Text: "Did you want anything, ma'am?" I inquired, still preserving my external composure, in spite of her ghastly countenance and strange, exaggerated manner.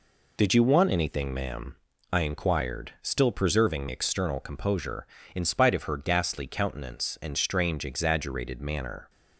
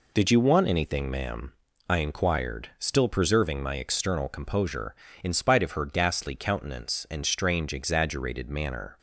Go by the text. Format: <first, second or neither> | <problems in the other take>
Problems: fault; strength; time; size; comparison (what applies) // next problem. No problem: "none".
second | skips "my"; at 3.8 s